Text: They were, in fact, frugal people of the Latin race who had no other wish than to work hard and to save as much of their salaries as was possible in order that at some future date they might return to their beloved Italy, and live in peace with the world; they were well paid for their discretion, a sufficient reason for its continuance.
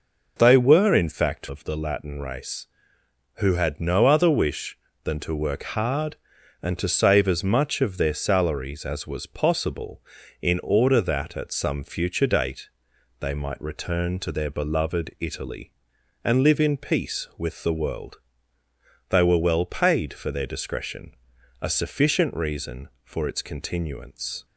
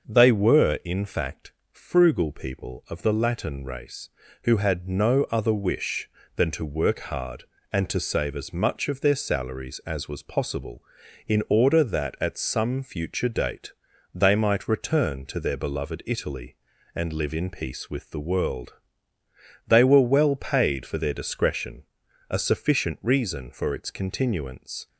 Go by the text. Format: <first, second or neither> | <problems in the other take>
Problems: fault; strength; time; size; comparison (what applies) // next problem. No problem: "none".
second | skips "frugal people"; at 1.4 s // pauses between "date" and "they"; noticeable; at 12.6 s; 0.50 s long; also in the second